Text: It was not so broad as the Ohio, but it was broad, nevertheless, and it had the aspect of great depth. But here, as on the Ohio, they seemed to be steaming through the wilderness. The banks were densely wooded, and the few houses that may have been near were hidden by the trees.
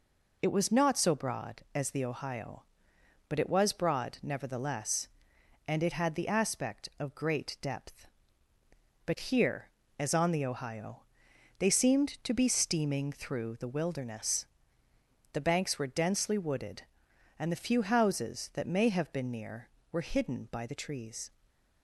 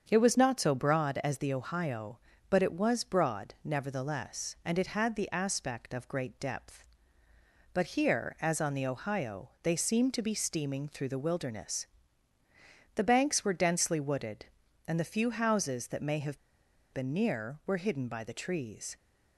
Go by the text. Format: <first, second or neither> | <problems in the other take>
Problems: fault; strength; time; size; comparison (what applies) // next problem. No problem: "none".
first | starts louder than the rest; strong; until 1.0 s; 7 dB // pauses between "have" and "been"; noticeable; at 16.3 s; 0.53 s long